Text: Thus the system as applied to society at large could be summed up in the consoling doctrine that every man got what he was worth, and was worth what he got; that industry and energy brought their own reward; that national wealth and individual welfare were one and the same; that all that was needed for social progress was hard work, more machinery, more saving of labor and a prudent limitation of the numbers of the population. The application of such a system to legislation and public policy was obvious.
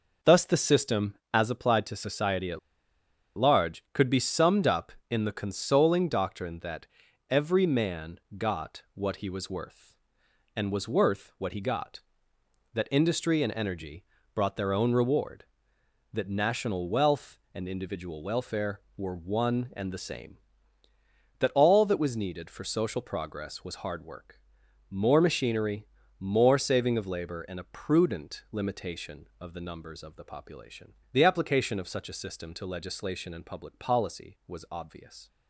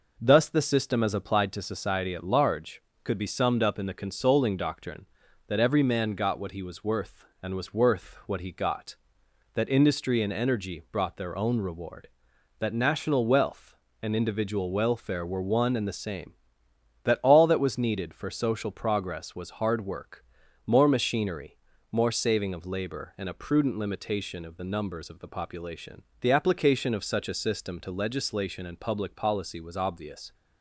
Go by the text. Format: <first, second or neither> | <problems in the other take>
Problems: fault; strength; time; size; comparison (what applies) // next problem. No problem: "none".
second | pauses between "at" and "large"; noticeable; at 2.5 s; 0.78 s long // pauses between "that" and "every"; at 6.8 s; 0.44 s long // pauses between "man" and "got"; slight; at 8.1 s; 0.20 s long // pauses between "energy" and "brought"; slight; at 14.0 s; 0.30 s long